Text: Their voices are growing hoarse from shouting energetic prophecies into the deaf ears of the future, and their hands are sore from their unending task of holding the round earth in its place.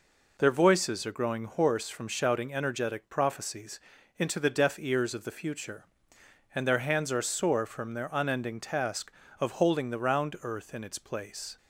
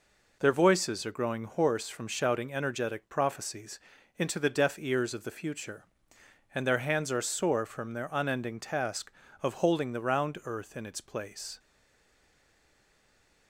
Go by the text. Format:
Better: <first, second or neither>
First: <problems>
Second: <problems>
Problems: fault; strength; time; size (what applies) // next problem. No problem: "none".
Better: first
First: pauses between "prophecies" and "into"; at 3.7 s; 0.38 s long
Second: pauses between "prophecies" and "into"; at 3.7 s; 0.38 s long // stays silent after the last word; noticeable; from 11.5 s on; 1.9 s long